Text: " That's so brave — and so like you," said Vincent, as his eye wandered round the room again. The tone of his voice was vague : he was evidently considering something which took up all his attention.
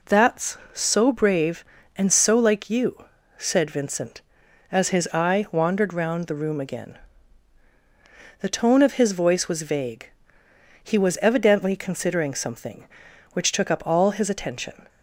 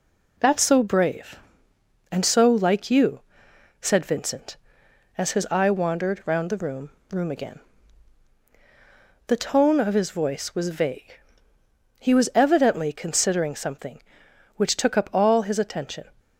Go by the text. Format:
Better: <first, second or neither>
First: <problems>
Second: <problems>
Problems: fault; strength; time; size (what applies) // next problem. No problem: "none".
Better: first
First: none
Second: says "room" twice; at 7.0 s